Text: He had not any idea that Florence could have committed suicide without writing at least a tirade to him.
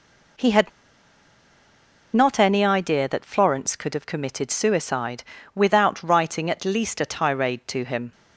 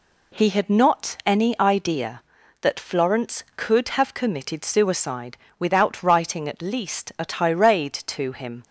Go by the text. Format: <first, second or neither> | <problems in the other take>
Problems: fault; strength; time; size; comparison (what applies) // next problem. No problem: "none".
second | pauses between "had" and "not"; strong; at 0.7 s; 1.4 s long // pauses between "suicide" and "without"; slight; at 5.2 s; 0.32 s long; slight in the second